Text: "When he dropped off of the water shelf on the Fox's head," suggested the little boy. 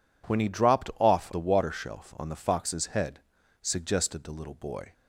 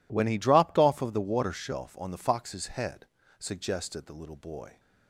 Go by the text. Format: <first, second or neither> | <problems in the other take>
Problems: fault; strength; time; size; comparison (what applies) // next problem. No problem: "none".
second | skips "of"; at 1.3 s